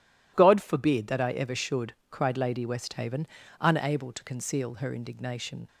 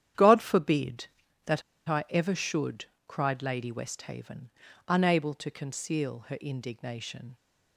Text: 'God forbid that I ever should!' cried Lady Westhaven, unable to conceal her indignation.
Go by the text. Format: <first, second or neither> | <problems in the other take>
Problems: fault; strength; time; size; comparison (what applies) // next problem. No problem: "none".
first | starts louder than the rest; strong; until 1.5 s; 10 dB // pauses between "that" and "I"; slight; at 1.6 s; 0.27 s long